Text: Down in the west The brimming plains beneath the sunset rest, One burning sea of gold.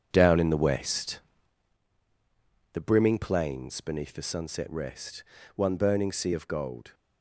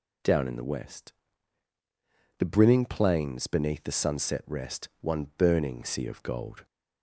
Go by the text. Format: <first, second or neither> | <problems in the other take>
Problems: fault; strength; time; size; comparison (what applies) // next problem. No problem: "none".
second | gets quieter; strong; throughout; 10 dB // pauses between "west" and "The"; strong; at 1.1 s; 1.5 s long; strong in the second